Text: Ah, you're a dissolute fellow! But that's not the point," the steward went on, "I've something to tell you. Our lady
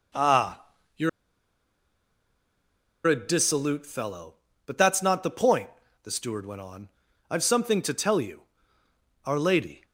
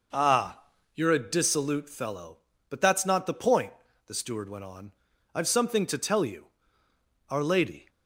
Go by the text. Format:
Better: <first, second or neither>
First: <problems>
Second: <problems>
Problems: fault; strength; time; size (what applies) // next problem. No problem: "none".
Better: second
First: pauses between "you're" and "a"; strong; at 1.0 s; 1.9 s long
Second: none